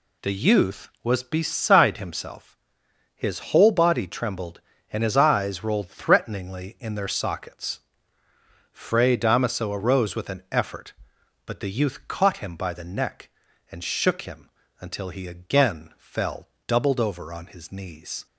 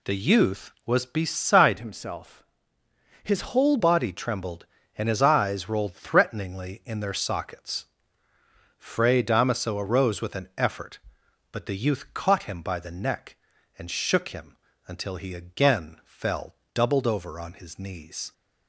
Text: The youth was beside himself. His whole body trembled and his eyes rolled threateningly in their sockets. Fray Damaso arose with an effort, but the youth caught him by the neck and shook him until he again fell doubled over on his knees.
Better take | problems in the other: first | changes voice from "himself" to "whole"; from 1.7 to 3.7 s; 2.0 s long // pauses between "him" and "until"; slight; at 14.5 s; 0.30 s long; slight in the first // pauses between "fell" and "doubled"; slight; at 16.5 s; 0.18 s long; slight in the first

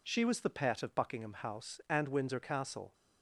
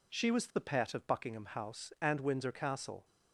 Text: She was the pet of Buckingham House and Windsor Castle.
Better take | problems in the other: neither | none

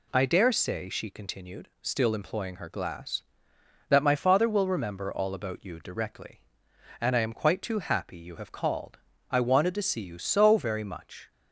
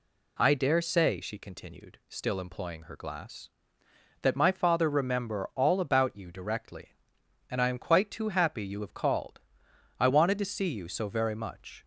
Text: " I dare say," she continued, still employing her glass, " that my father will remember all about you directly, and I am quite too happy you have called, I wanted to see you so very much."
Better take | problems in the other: first | skips "will"; at 4.8 s

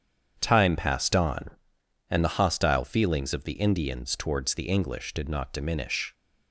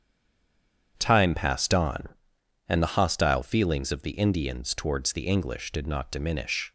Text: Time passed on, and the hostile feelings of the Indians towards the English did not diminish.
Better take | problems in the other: first | stays silent before the first word; slight; until 0.9 s; 0.9 s long // starts louder than the rest; strong; until 1.9 s; 8 dB; strong in the first

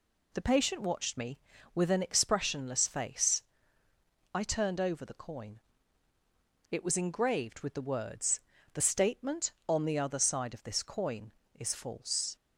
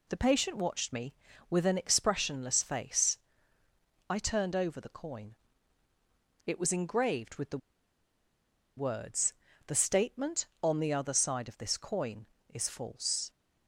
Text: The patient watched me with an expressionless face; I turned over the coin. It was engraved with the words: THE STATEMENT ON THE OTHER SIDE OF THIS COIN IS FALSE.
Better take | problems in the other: first | pauses between "the" and "words"; at 7.5 s; 1.1 s long

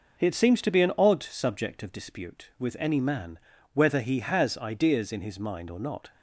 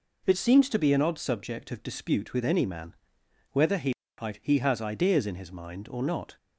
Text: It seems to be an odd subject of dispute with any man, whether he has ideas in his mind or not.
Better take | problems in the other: first | says "he" twice; at 4.4 s

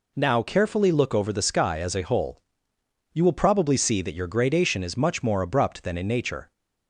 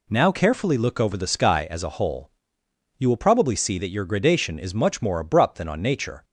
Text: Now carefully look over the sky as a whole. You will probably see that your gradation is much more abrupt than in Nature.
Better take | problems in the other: first | says "on" for "in"; at 5.6 s

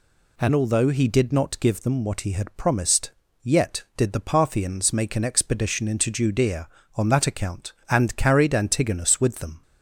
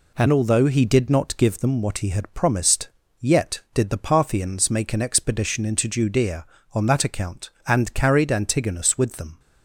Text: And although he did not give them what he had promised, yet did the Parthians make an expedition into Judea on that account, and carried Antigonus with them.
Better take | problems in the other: first | gets quieter; throughout; 3.5 dB

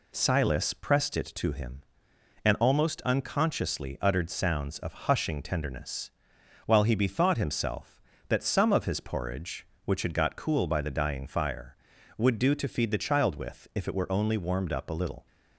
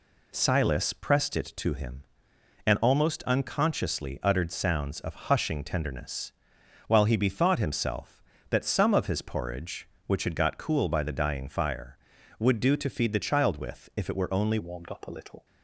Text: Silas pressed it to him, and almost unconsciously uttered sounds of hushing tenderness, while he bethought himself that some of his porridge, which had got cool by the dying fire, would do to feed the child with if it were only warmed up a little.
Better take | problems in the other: first | changes voice at "warmed"; from 14.5 s on; 0.9 s long

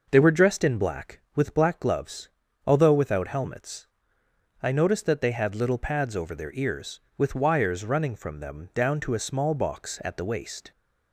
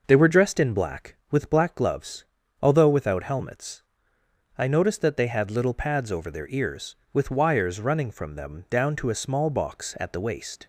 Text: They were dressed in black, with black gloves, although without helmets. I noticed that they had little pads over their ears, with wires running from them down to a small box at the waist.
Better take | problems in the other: neither | none

